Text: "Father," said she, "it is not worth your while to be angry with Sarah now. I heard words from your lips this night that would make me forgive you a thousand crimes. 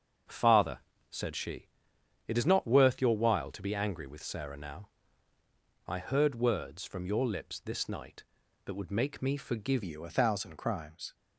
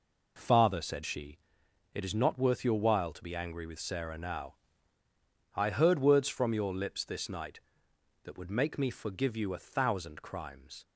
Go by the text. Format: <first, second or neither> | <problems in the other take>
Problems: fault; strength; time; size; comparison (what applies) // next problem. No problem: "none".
second | starts louder than the rest; strong; until 1.5 s; 7 dB // changes voice at "you"; from 9.8 s on; 1.3 s long